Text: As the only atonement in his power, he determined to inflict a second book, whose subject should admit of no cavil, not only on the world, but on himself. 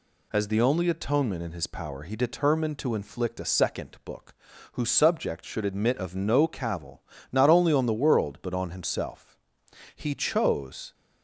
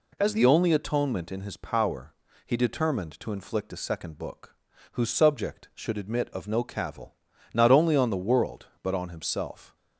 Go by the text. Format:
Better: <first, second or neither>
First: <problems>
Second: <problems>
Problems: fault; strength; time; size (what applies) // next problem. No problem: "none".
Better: second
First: goes on to say "He chose"; noticeable; from 9.9 s on; 0.98 s long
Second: none